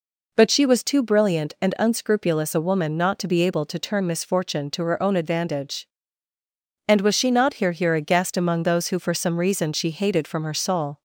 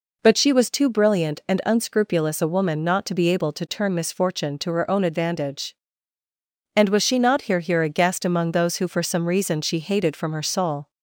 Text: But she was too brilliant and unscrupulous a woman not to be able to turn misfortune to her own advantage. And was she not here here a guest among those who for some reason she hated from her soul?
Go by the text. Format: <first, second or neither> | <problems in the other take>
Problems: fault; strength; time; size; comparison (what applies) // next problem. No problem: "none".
neither | none